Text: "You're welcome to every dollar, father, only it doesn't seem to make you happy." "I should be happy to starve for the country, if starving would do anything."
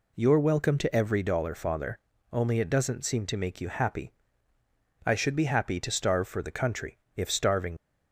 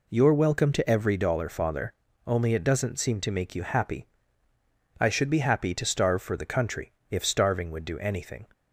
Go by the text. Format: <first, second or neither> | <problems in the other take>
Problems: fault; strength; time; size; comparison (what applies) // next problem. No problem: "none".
second | stops before "would do anything"; at 7.7 s